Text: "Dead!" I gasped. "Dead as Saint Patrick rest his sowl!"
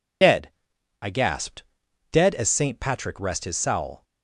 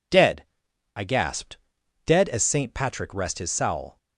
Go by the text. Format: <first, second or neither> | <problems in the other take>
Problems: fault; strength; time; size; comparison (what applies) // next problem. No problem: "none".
second | loses the start of "Dead"; at 0.2 s; 40 ms